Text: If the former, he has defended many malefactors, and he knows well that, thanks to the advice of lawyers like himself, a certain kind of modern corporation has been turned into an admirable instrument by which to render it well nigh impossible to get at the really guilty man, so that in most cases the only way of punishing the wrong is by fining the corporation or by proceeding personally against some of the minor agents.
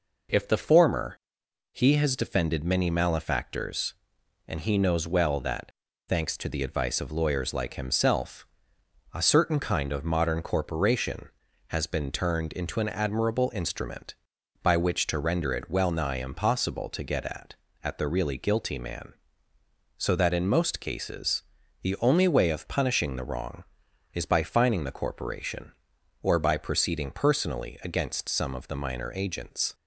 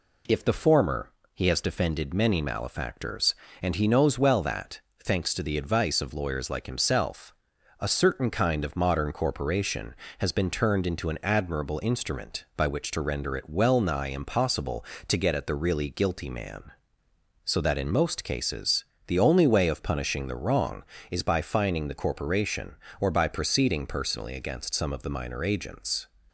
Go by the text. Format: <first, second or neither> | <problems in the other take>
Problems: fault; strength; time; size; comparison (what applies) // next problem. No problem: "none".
second | says "at" twice; at 17.8 s // pauses between "cases" and "the"; at 21.4 s; 0.40 s long; slight in the second